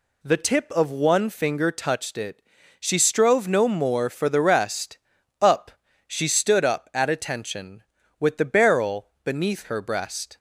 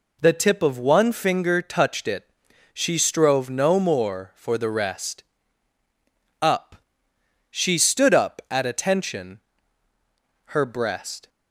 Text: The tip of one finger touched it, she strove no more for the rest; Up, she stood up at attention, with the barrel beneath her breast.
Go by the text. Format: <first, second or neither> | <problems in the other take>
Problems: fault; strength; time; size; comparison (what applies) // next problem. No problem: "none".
first | skips "with the barrel beneath"; at 9.9 s